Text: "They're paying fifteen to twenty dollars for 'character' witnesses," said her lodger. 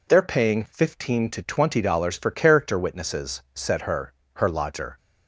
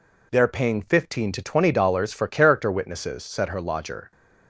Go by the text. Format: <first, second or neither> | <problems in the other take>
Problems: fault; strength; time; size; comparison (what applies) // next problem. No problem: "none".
second | says "her" twice; at 4.3 s